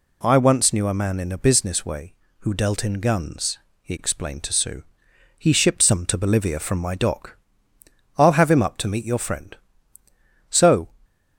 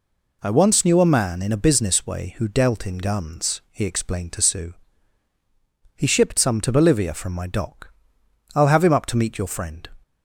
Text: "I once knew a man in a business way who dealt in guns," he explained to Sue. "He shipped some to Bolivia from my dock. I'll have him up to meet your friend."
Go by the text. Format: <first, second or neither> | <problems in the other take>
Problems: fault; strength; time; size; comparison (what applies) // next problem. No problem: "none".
second | goes on to say "So"; slight; from 10.4 s on; 0.38 s long